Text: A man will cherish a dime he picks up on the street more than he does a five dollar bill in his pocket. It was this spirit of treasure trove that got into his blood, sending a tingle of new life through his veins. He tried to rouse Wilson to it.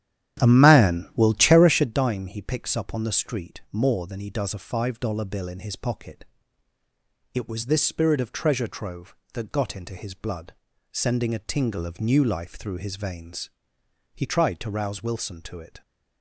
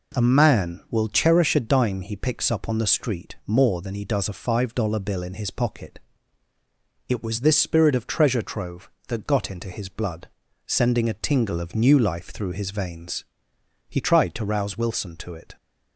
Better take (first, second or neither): second